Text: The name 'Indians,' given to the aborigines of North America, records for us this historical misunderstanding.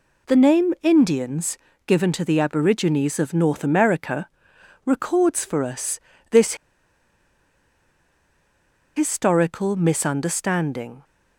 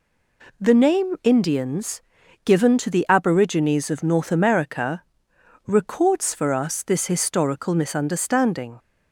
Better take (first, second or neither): second